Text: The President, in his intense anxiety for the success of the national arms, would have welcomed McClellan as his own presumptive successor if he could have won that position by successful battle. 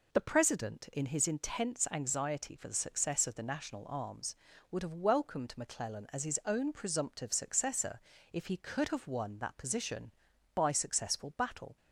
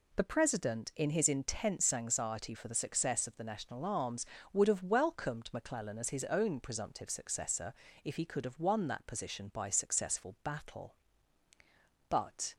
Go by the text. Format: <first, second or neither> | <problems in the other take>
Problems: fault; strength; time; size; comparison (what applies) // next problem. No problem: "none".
first | pauses between "successor" and "if"; slight; at 7.7 s; 0.32 s long; slight in the first // goes on to say "But"; slight; from 12.1 s on; 0.44 s long